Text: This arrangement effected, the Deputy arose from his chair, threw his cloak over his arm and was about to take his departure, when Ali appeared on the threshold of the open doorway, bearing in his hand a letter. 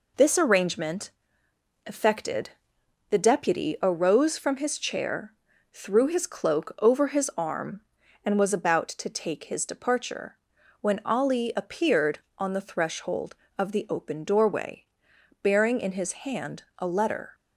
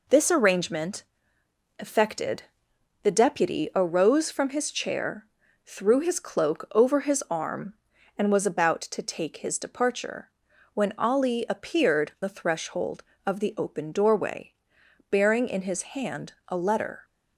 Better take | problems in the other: first | pauses between "arrangement" and "effected"; noticeable; at 1.0 s; 0.76 s long; noticeable in the first // skips "on"; at 12.1 s

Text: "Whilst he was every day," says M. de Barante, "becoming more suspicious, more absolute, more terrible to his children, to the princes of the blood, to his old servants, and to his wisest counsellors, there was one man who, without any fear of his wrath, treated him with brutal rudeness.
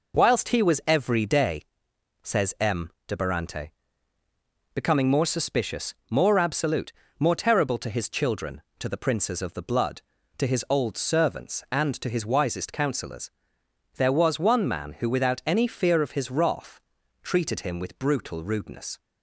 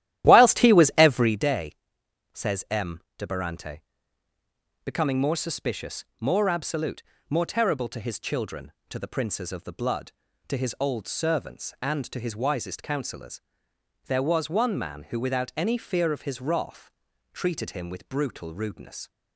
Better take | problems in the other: first | starts louder than the rest; strong; until 1.4 s; 13 dB

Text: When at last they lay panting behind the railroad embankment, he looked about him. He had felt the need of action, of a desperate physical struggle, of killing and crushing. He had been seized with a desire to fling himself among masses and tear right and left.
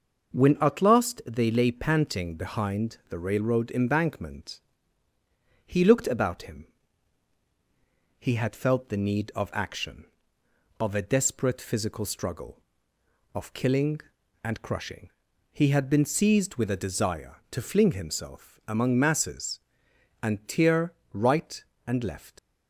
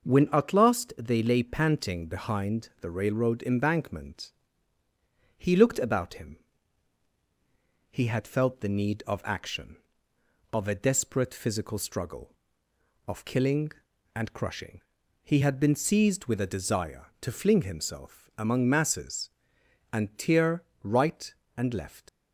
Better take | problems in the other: neither | pauses between "tear" and "right"; slight; the same in both

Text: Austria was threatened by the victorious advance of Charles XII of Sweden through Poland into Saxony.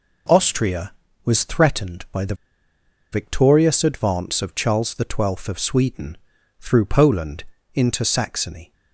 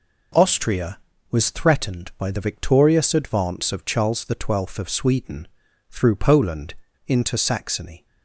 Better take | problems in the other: second | pauses between "the" and "victorious"; noticeable; at 2.3 s; 0.77 s long // pauses between "Sweden" and "through"; at 6.1 s; 0.44 s long; also in the second // pauses between "Poland" and "into"; slight; at 7.4 s; 0.30 s long; slight in the second

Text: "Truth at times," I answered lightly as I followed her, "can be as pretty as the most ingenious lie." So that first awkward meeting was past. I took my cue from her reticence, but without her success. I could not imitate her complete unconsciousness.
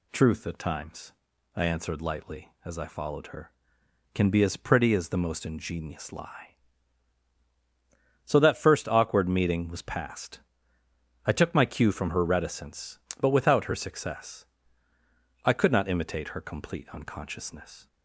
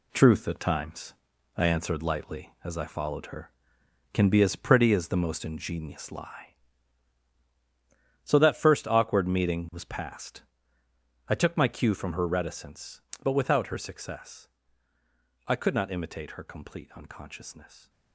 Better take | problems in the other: first | gets quieter; strong; throughout; 8 dB

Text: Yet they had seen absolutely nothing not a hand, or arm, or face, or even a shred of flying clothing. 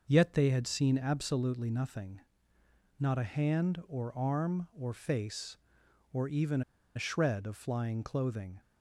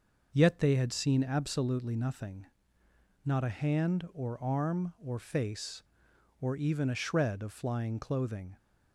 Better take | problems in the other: second | pauses between "nothing" and "not"; noticeable; at 2.1 s; 0.80 s long; noticeable in the second // pauses between "even" and "a"; slight; at 6.6 s; 0.34 s long

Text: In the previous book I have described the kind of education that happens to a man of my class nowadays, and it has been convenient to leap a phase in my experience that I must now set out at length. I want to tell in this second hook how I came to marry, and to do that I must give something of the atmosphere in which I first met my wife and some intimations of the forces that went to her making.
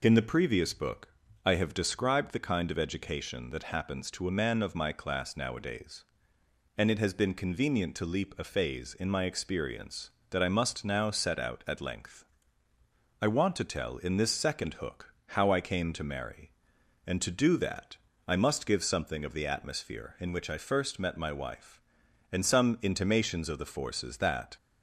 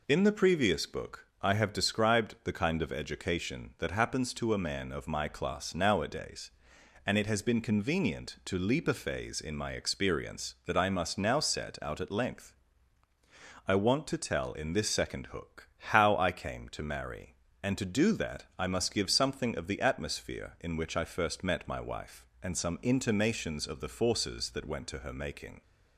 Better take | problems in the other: second | pauses between "book" and "I"; at 1.0 s; 0.38 s long; slight in the second // pauses between "that" and "I"; slight; at 17.9 s; 0.32 s long // stops before "went to her making"; at 24.5 s

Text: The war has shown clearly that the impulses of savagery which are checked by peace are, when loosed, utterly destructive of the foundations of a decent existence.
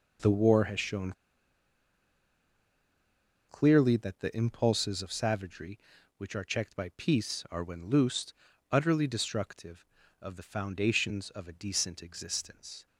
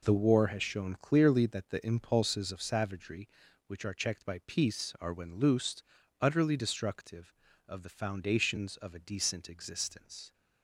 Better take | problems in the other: second | pauses between "shown" and "clearly"; strong; at 1.1 s; 2.3 s long

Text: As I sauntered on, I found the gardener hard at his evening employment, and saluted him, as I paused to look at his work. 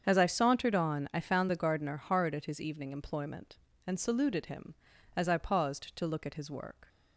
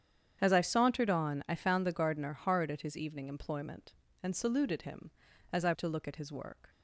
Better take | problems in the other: first | starts louder than the rest; strong; until 1.4 s; 8.5 dB; strong in the first // skips "paused"; at 5.7 s

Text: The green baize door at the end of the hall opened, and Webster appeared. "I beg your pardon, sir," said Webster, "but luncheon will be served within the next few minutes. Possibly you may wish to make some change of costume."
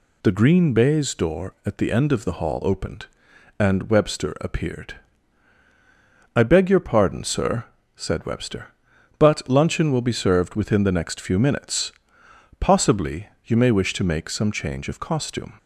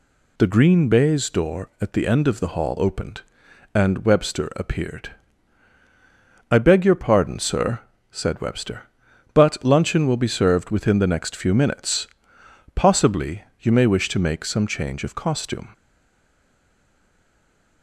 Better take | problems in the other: first | pauses between "Possibly" and "you"; slight; at 13.4 s; 0.16 s long; slight in the first // stays silent after the last word; noticeable; from 15.7 s on; 2.1 s long

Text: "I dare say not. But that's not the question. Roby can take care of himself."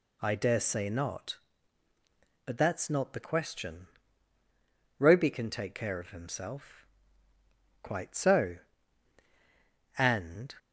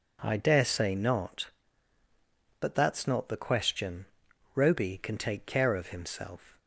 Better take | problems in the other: second | goes on to say "Quite so And"; strong; from 7.8 s on; 2.7 s long

